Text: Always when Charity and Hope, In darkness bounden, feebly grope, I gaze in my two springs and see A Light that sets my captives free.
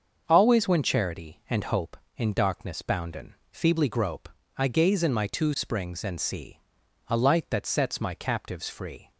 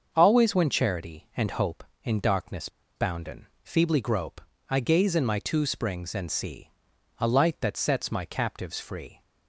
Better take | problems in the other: first | starts louder than the rest; until 1.1 s; 6.5 dB; also in the first // pauses between "darkness" and "bounden"; slight; at 2.6 s; 0.28 s long // pauses between "see" and "A"; noticeable; at 6.6 s; 0.48 s long; noticeable in the first

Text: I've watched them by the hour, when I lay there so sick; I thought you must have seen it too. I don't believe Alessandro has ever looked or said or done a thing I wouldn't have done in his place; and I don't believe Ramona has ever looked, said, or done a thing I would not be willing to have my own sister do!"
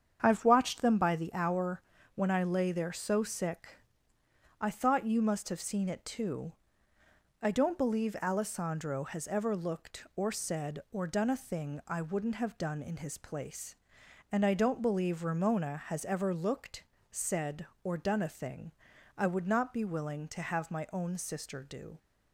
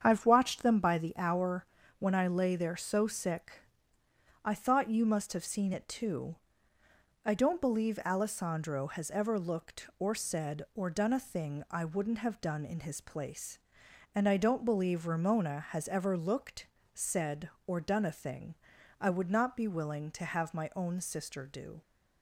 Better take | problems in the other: neither | starts louder than the rest; strong; the same in both // pauses between "thing" and "I"; the same in both

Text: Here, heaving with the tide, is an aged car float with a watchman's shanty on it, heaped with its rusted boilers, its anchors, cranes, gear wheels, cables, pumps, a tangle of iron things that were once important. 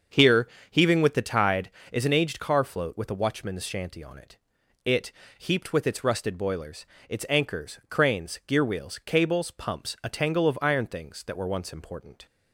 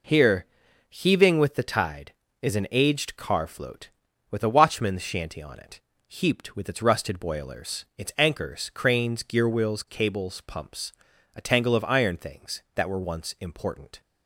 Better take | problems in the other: second | starts louder than the rest; until 1.3 s; 7 dB // says "it" twice; at 4.8 s

